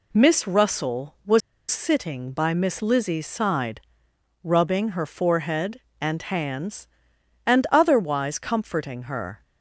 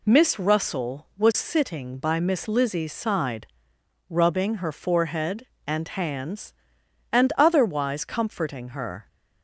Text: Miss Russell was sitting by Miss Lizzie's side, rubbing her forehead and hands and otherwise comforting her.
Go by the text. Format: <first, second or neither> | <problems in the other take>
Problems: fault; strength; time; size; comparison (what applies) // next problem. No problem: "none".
second | pauses between "was" and "sitting"; slight; at 1.4 s; 0.29 s long